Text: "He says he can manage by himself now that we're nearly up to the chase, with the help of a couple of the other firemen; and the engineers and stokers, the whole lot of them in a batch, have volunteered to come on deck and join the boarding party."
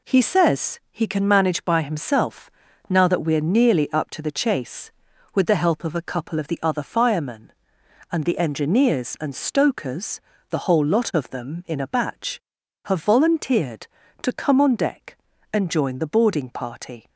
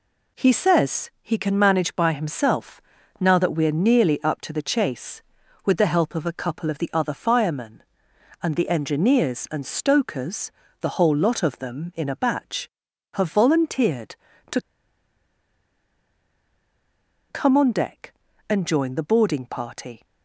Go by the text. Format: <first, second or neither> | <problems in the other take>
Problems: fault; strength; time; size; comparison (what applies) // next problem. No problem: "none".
first | pauses between "himself" and "now"; at 2.8 s; 0.40 s long; also in the first // pauses between "to" and "come"; strong; at 14.5 s; 2.7 s long